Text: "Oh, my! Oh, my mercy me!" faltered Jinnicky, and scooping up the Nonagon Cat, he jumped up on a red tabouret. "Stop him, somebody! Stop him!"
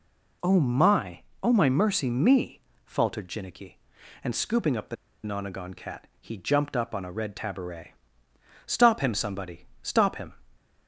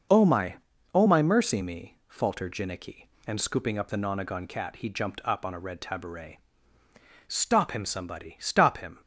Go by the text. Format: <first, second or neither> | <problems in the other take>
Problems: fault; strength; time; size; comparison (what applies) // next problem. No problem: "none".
second | pauses between "the" and "Nonagon"; slight; at 4.9 s; 0.28 s long